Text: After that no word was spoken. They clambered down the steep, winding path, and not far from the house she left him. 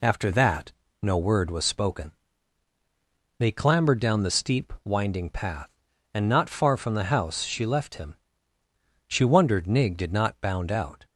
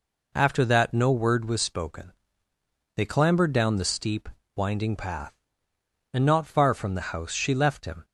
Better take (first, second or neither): second